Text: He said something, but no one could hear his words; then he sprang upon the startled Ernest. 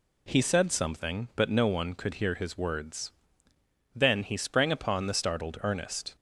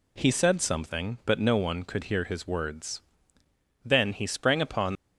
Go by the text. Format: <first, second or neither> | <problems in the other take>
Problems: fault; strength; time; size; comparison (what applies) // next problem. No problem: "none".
first | stops before "the startled Ernest"; at 4.9 s